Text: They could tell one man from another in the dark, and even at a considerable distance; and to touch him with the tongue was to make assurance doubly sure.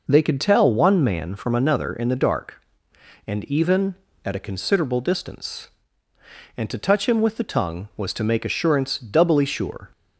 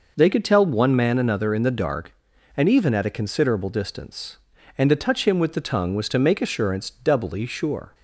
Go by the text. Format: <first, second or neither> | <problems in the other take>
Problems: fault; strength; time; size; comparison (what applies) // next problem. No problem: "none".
first | skips "from"; at 1.1 s